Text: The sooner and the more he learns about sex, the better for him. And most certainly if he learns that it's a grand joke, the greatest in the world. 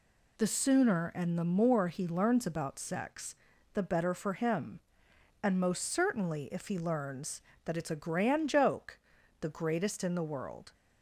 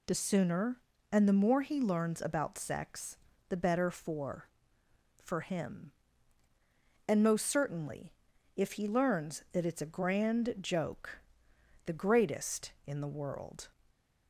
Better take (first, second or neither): first